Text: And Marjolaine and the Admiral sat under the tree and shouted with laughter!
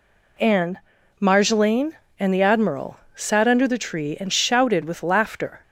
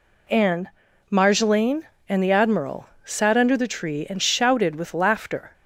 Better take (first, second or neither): neither